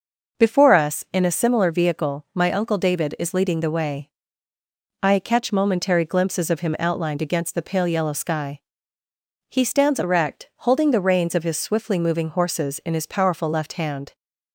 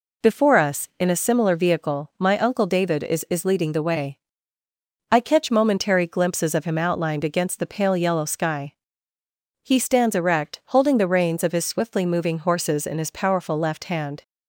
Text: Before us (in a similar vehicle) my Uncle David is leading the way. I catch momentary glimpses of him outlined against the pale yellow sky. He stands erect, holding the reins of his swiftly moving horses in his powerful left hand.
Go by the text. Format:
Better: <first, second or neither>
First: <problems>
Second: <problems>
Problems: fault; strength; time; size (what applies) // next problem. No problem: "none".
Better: first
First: none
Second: says "is" twice; at 3.2 s